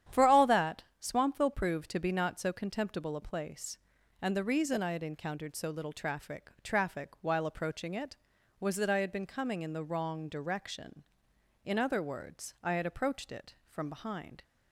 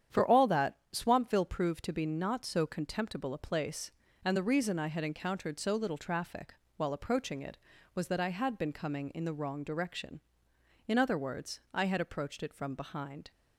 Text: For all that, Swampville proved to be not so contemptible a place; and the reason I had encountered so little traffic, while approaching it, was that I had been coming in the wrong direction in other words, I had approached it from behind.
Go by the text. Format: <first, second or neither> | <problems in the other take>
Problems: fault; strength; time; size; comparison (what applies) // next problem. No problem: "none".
second | starts louder than the rest; strong; until 1.2 s; 10 dB; strong in the second // says "traffic" twice; at 6.6 s